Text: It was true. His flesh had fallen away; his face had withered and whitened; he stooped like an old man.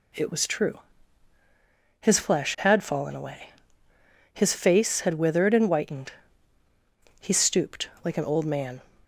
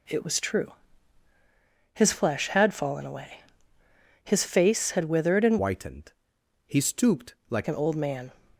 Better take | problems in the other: first | changes voice from "whitened" to "like"; from 5.5 to 7.6 s; 2.1 s long

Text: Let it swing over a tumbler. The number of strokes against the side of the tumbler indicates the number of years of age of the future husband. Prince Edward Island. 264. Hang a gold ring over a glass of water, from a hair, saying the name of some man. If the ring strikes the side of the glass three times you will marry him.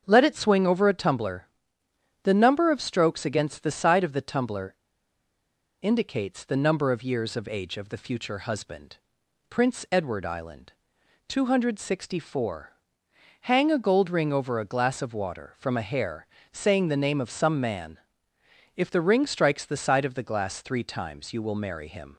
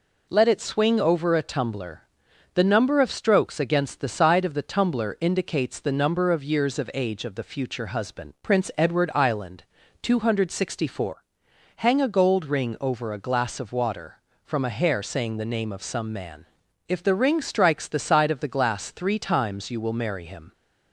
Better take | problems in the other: second | starts louder than the rest; until 1.0 s; 7 dB // pauses between "tumbler" and "indicates"; at 4.7 s; 1.0 s long

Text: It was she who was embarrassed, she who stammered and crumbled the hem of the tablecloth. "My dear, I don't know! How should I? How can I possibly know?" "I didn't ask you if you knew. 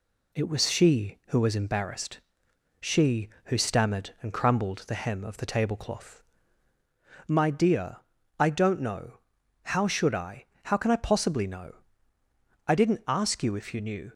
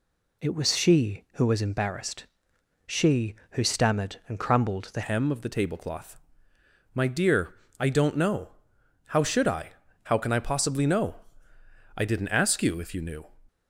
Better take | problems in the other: first | changes voice at "hem"; from 5.0 s on; 8.2 s long

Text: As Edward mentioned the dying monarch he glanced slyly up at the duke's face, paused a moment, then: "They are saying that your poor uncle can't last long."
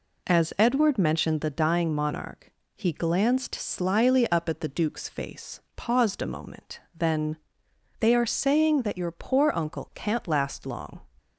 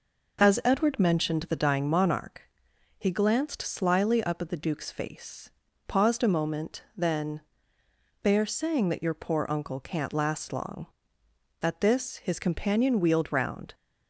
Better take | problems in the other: first | pauses between "monarch" and "he"; noticeable; at 2.4 s; 0.54 s long; slight in the first // goes on to say "At this his companion wheeled round"; strong; from 11.5 s on; 2.1 s long

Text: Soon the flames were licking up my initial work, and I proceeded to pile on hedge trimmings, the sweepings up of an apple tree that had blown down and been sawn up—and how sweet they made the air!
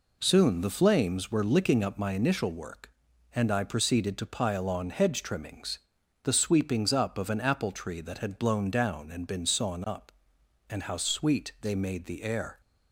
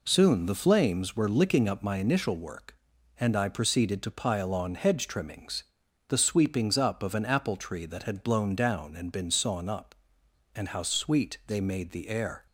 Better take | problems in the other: neither | none

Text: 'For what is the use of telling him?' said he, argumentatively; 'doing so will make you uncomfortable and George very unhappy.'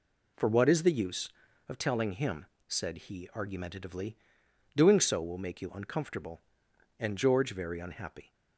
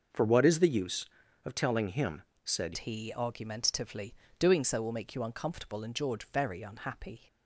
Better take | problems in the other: first | starts louder than the rest; until 1.5 s; 6 dB // changes voice at "he"; from 2.7 s on; 4.5 s long

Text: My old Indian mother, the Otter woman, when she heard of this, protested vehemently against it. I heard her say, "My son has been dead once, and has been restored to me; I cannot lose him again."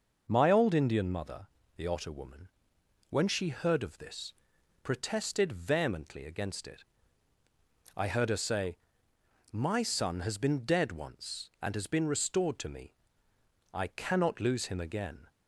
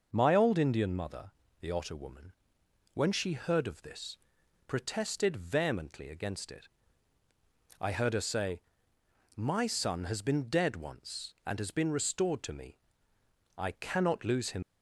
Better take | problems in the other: first | stops before "again"; at 14.6 s

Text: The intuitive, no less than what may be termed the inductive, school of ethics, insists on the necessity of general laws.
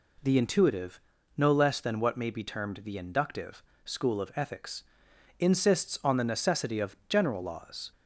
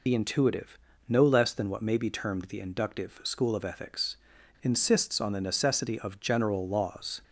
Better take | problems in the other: first | loses the start of "The"; at 0.0 s; 50 ms

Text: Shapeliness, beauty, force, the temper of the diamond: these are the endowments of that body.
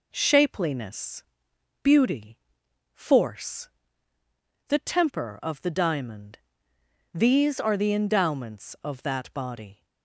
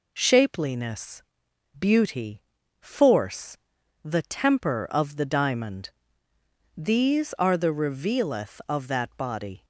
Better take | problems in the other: first | says "revealeth" for "endowments"; at 7.7 s

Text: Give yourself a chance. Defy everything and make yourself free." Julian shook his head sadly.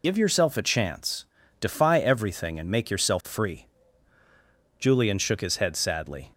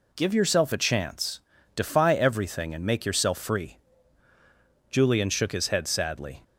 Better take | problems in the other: second | loses the start of "Give"; at 0.0 s; 65 ms

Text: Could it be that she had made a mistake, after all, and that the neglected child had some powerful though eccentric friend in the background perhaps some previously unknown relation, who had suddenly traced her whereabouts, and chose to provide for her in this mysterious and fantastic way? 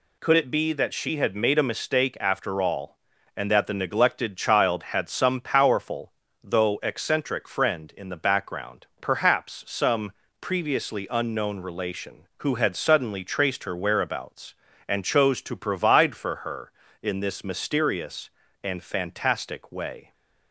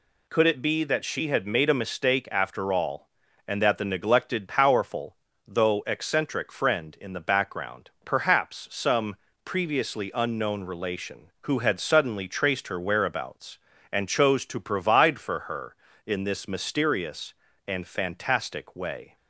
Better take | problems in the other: first | skips "child had some"; at 4.4 s // pauses between "powerful" and "though"; slight; at 5.1 s; 0.34 s long; slight in the first // pauses between "some" and "previously"; slight; at 9.1 s; 0.30 s long; slight in the first

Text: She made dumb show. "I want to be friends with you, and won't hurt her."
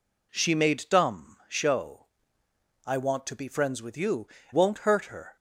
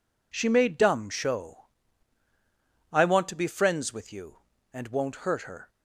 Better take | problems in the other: second | skips "and"; at 4.4 s

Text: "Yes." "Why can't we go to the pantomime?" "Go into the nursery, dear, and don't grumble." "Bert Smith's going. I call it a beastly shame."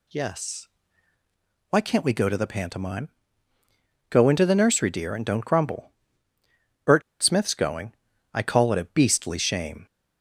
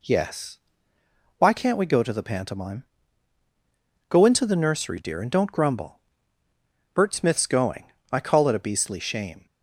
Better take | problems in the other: second | pauses between "Bert" and "Smith's"; slight; at 7.0 s; 0.19 s long

